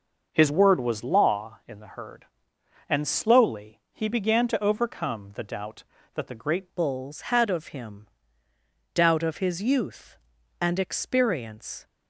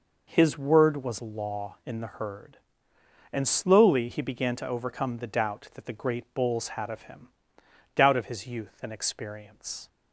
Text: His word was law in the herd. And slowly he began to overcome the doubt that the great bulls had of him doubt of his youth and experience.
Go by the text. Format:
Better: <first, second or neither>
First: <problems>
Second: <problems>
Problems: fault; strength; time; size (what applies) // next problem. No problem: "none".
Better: second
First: changes voice at "bulls"; from 6.7 s on; 5.1 s long // pauses between "him" and "doubt"; noticeable; at 8.0 s; 0.88 s long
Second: pauses between "him" and "doubt"; noticeable; at 7.2 s; 0.68 s long